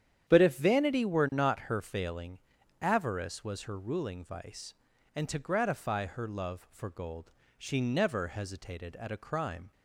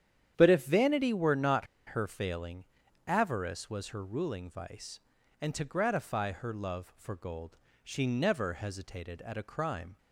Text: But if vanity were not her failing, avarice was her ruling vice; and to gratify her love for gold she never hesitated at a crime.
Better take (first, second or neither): first